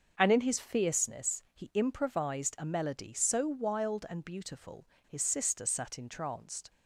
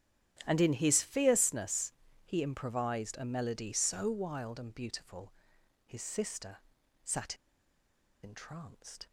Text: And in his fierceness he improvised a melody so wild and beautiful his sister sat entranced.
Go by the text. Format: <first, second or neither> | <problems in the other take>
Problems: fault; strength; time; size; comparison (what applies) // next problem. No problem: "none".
first | starts louder than the rest; strong; until 1.4 s; 10.5 dB; also in the first // pauses between "fierceness" and "he"; slight; at 1.9 s; 0.32 s long // pauses between "beautiful" and "his"; noticeable; at 5.3 s; 0.54 s long; slight in the first // pauses between "sister" and "sat"; noticeable; at 6.5 s; 0.46 s long // pauses between "sat" and "entranced"; noticeable; at 7.3 s; 0.87 s long